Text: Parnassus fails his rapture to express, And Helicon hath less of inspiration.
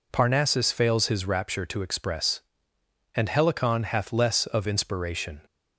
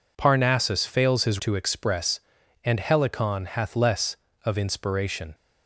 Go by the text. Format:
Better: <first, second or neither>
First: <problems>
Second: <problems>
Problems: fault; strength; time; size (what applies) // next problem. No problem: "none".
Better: first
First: none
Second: skips "rapture"; at 1.3 s